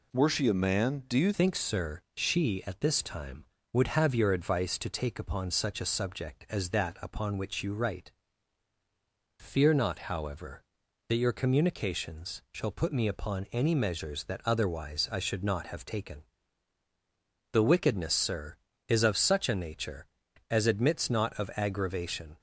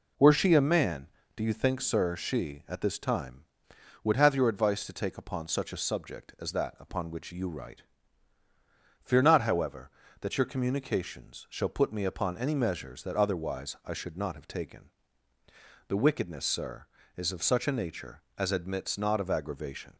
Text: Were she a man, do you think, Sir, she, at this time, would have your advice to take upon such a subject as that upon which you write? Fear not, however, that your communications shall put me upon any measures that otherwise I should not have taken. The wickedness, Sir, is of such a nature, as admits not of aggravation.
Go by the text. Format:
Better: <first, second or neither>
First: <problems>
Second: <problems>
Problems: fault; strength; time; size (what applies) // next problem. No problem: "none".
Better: second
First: changes voice at "think"; from 1.3 s on; 21.0 s long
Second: none